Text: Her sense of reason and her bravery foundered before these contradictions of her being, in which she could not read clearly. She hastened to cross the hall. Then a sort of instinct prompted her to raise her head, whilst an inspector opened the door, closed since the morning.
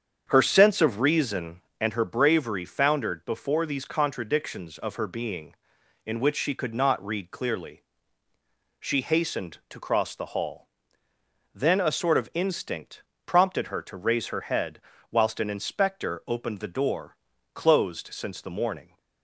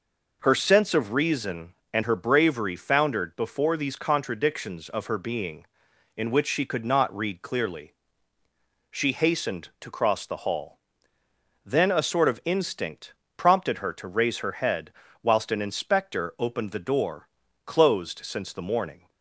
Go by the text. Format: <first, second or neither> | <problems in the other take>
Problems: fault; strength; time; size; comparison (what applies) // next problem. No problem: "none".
second | starts louder than the rest; strong; until 1.9 s; 7.5 dB // pauses between "instinct" and "prompted"; slight; at 13.0 s; 0.24 s long; slight in the second